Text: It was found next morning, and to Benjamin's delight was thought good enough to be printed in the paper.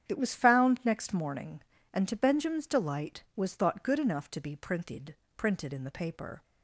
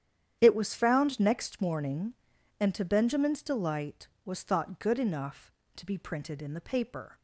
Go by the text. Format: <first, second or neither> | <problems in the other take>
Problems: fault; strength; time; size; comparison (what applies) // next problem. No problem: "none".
second | starts louder than the rest; strong; until 1.1 s; 9 dB; strong in the second // says "printed" twice; at 5.3 s